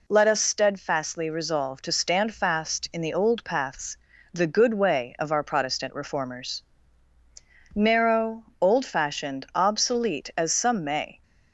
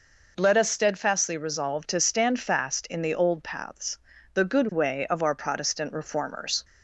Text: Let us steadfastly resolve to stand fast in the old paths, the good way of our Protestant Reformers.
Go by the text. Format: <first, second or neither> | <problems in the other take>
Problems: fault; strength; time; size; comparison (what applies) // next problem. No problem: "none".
second | goes on to say "Narrow old fashioned obsolete as some may"; strong; from 7.7 s on; 3.4 s long